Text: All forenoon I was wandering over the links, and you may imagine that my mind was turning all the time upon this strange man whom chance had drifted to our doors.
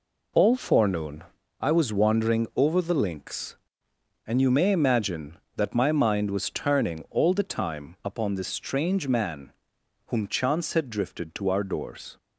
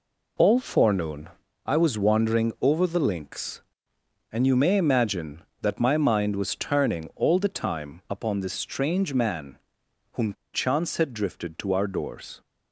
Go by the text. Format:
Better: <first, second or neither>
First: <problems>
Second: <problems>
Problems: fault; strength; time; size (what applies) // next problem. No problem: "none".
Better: first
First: pauses between "forenoon" and "I"; slight; at 1.2 s; 0.36 s long // pauses between "man" and "whom"; noticeable; at 9.5 s; 0.56 s long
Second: pauses between "forenoon" and "I"; slight; at 1.2 s; 0.36 s long // pauses between "man" and "whom"; noticeable; at 9.5 s; 0.56 s long // pauses between "whom" and "chance"; slight; at 10.3 s; 0.18 s long